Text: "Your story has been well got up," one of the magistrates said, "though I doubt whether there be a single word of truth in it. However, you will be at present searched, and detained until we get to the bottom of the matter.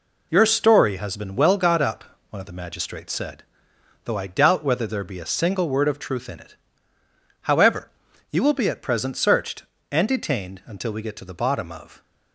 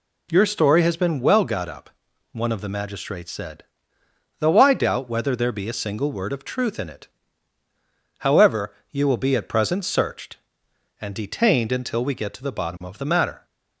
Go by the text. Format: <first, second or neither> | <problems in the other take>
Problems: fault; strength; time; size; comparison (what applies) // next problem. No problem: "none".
second | stops before "the matter"; at 12.0 s